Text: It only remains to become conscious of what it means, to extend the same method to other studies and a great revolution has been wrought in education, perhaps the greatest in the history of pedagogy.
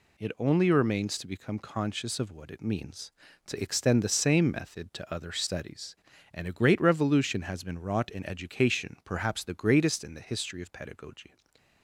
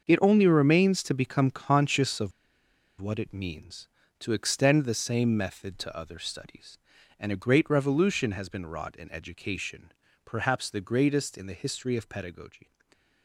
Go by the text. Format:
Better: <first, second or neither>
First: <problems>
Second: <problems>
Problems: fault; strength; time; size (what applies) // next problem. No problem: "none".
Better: first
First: none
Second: starts louder than the rest; until 1.0 s; 6.5 dB // pauses between "of" and "what"; noticeable; at 2.3 s; 0.68 s long